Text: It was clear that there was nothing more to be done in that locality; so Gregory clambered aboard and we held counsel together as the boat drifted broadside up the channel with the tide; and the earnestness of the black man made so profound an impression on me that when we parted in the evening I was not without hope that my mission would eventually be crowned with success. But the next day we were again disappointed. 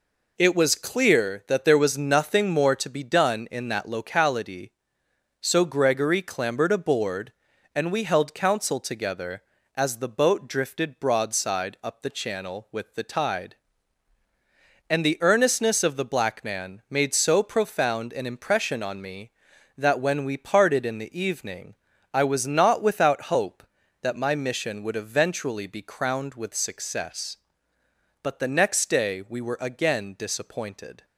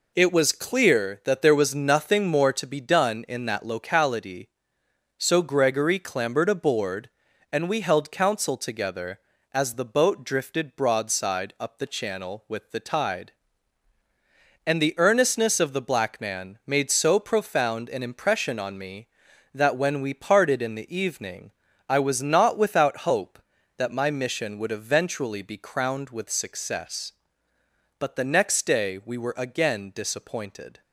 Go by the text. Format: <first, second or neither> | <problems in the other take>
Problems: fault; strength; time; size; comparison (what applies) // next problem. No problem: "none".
neither | pauses between "evening" and "I"; slight; the same in both